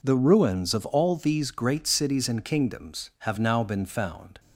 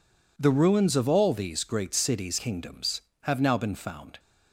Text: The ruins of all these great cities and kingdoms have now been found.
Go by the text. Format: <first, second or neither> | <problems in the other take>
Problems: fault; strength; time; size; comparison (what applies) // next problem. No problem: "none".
first | skips "and"; at 2.3 s